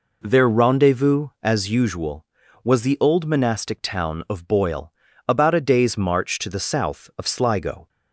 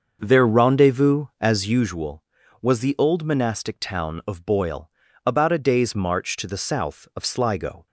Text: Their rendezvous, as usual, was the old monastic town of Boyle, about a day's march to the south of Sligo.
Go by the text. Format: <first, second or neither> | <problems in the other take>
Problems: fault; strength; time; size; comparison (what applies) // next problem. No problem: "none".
first | starts louder than the rest; until 2.0 s; 6.5 dB